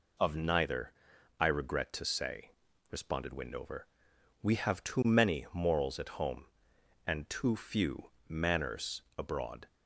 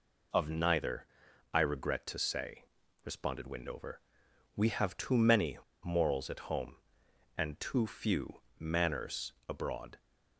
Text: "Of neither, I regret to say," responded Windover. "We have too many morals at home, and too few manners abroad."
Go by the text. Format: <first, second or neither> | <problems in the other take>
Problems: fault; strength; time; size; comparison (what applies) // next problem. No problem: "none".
first | pauses between "many" and "morals"; slight; at 5.5 s; 0.26 s long // pauses between "few" and "manners"; slight; at 8.4 s; 0.18 s long; slight in the first // pauses between "manners" and "abroad"; slight; at 9.3 s; 0.16 s long; slight in the first